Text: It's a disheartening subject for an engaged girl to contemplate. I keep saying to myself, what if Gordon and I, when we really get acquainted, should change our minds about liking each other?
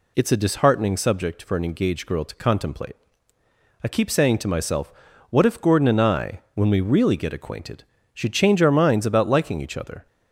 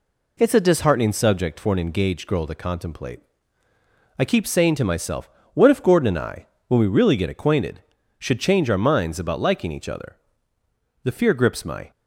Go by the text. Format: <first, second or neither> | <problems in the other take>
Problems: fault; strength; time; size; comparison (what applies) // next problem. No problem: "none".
first | goes on to say "The fear grips my"; noticeable; from 11.0 s on; 0.88 s long